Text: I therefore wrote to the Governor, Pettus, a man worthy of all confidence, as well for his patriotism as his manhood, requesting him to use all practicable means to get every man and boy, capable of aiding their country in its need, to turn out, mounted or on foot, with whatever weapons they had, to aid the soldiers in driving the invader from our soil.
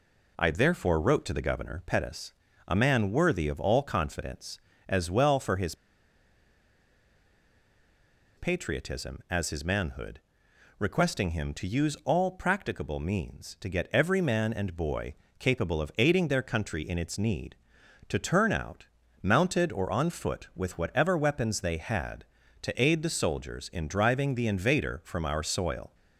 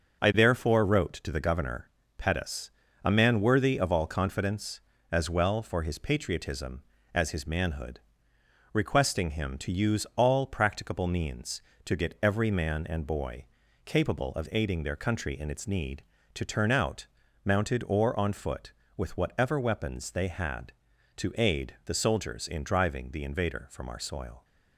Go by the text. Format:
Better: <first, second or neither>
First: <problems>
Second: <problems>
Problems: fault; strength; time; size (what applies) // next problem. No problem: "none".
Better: second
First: pauses between "his" and "patriotism"; strong; at 5.7 s; 2.6 s long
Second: none